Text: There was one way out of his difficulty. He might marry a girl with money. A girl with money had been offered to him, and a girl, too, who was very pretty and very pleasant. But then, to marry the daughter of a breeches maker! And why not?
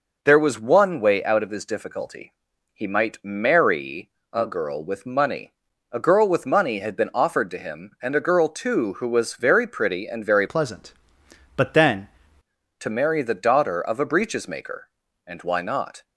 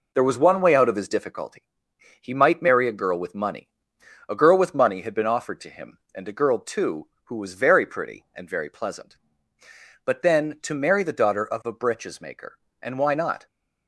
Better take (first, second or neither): second